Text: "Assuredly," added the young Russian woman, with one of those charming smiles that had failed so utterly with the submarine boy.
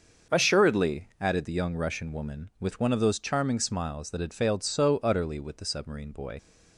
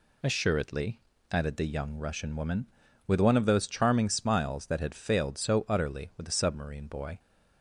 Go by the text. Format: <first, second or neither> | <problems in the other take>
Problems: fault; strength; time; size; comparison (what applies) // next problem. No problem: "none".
second | starts louder than the rest; until 1.4 s; 6.5 dB // leaves "boy" unfinished; at 6.3 s; 45 ms